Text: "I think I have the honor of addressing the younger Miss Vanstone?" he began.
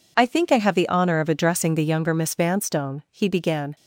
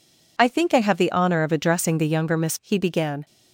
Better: first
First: none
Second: skips "Vanstone"; at 2.5 s

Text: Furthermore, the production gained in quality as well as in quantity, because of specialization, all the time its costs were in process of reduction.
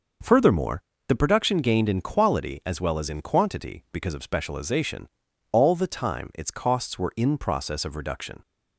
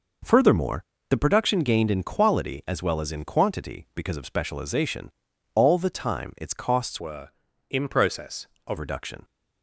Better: first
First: none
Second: changes voice from "were" to "of"; from 6.9 to 8.7 s; 1.8 s long

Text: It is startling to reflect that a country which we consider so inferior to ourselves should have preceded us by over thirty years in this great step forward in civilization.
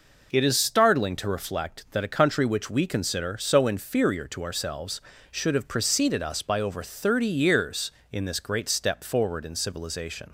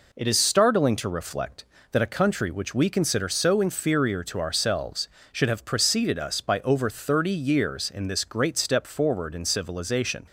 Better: neither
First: none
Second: none

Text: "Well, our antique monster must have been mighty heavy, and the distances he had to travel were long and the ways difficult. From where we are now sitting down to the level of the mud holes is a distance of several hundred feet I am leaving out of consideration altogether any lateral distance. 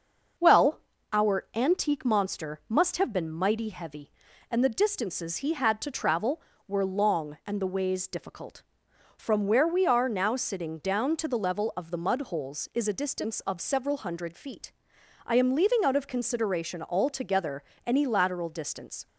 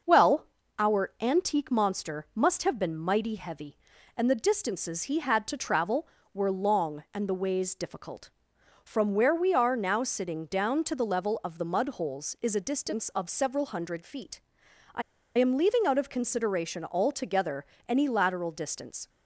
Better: first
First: starts louder than the rest; noticeable; until 1.7 s; 6 dB // pauses between "feet" and "I"; noticeable; at 14.7 s; 0.52 s long // pauses between "altogether" and "any"; slight; at 17.6 s; 0.24 s long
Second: starts louder than the rest; noticeable; until 1.4 s; 6 dB // pauses between "feet" and "I"; noticeable; at 14.4 s; 0.52 s long // pauses between "I" and "am"; at 15.0 s; 0.36 s long // pauses between "altogether" and "any"; slight; at 17.6 s; 0.24 s long

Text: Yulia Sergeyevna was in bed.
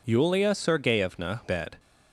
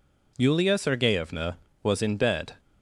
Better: second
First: skips "was in"; at 1.4 s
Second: none

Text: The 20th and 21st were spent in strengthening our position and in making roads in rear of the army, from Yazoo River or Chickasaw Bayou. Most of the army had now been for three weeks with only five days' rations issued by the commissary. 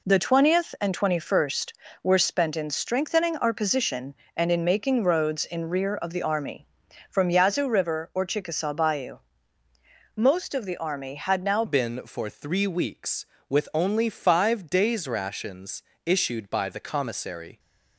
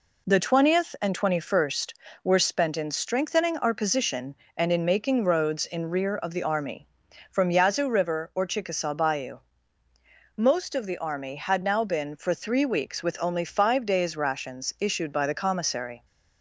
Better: second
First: changes voice at "been"; from 11.6 s on; 5.9 s long // pauses between "rations" and "issued"; slight; at 15.8 s; 0.22 s long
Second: none

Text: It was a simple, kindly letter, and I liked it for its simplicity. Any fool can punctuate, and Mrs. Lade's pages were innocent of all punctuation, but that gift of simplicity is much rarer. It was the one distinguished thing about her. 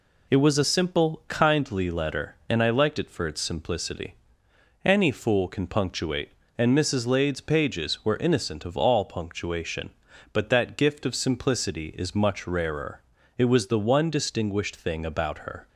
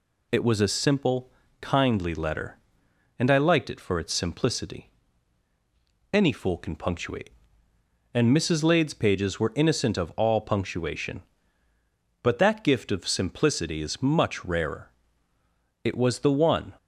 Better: first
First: none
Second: stops before "distinguished thing about her"; at 16.7 s

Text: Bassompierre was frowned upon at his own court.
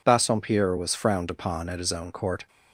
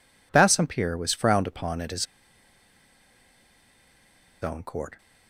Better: first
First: none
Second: pauses between "his" and "own"; strong; at 2.0 s; 2.3 s long

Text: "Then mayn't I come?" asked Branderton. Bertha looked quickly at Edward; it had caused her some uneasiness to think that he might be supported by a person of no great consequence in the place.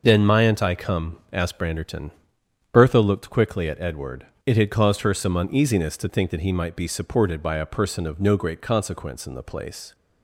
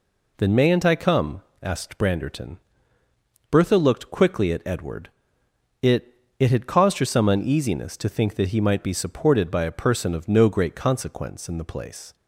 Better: first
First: none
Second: says "it" twice; at 6.3 s

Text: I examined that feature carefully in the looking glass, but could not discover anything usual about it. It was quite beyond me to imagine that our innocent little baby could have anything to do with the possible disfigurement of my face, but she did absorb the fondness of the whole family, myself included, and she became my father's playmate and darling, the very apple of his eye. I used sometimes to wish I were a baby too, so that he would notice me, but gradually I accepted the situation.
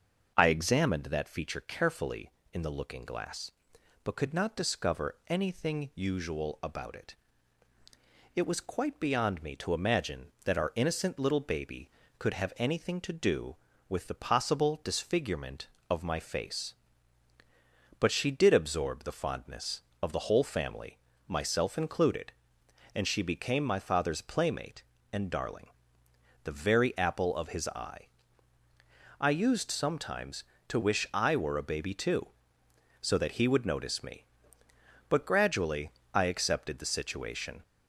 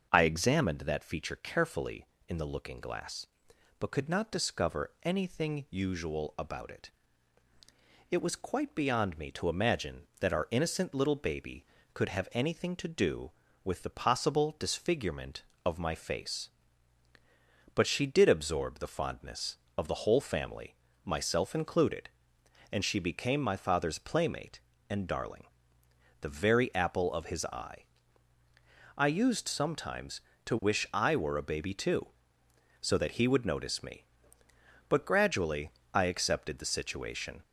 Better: neither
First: starts louder than the rest; until 1.3 s; 6.5 dB // pauses between "gradually" and "I"; slight; at 35.8 s; 0.24 s long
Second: starts louder than the rest; until 1.1 s; 6.5 dB // pauses between "gradually" and "I"; slight; at 35.6 s; 0.24 s long

